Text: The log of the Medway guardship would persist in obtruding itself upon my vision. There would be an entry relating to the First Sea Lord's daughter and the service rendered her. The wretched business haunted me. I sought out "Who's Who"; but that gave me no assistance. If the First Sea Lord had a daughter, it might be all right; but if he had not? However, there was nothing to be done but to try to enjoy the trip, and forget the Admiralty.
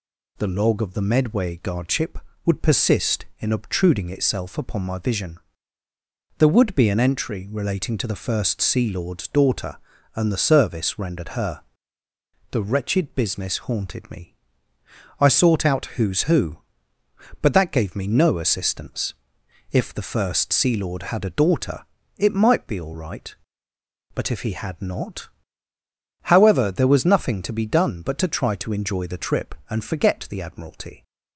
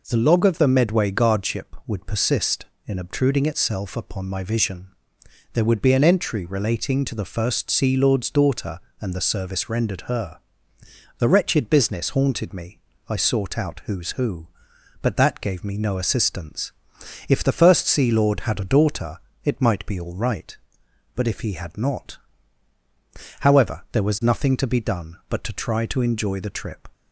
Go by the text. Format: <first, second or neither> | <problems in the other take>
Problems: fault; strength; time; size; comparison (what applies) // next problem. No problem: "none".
first | stops before "and forget the Admiralty"; at 26.9 s